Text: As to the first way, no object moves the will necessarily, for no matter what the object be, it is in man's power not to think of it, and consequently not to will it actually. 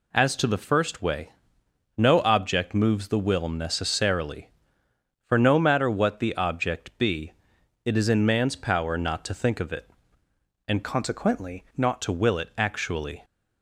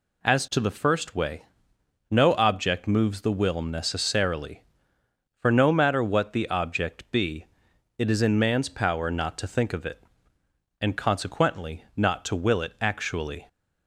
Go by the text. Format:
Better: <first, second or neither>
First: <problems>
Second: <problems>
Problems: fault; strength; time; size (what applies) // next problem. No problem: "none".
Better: second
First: changes voice from "consequently" to "not"; from 10.8 to 12.0 s; 1.2 s long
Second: none